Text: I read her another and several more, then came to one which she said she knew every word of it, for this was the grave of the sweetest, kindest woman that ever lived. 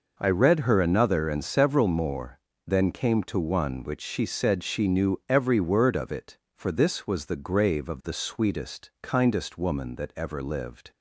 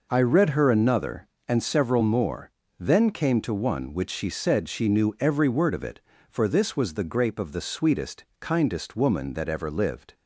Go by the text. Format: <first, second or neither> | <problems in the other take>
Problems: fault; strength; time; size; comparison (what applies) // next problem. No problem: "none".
first | says "grape" for "grave"; at 7.0 s